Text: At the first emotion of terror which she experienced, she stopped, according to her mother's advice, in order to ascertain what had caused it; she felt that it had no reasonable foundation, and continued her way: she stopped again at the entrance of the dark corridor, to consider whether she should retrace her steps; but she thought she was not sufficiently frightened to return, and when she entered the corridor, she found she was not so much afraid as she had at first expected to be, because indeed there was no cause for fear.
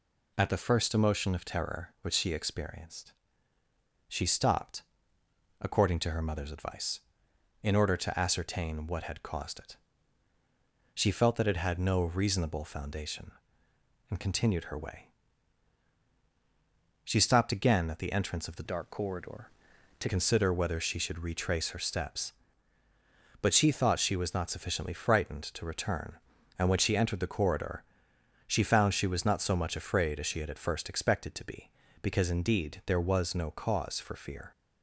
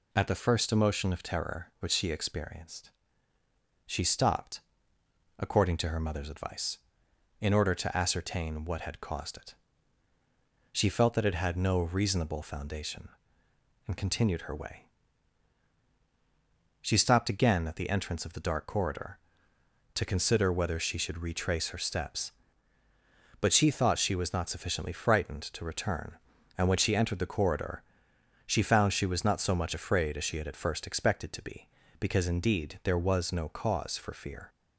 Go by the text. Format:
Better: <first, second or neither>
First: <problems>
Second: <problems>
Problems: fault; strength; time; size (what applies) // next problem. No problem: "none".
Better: second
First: changes voice from "dark" to "to"; from 18.6 to 20.0 s; 1.4 s long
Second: none